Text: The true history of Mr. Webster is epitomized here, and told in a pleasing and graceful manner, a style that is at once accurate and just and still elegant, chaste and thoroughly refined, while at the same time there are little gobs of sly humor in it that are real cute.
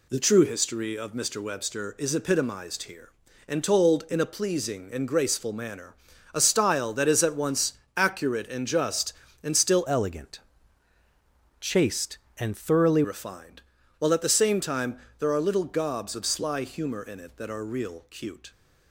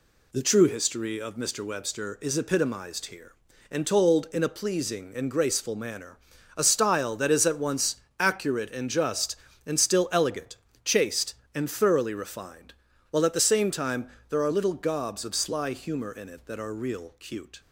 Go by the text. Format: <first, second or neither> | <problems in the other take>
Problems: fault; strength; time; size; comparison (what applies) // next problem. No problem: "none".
second | pauses between "once" and "accurate"; slight; at 7.7 s; 0.24 s long; slight in the second // changes voice from "elegant" to "thoroughly"; from 9.8 to 13.0 s; 3.2 s long // pauses between "time" and "there"; slight; at 14.9 s; 0.22 s long; slight in the second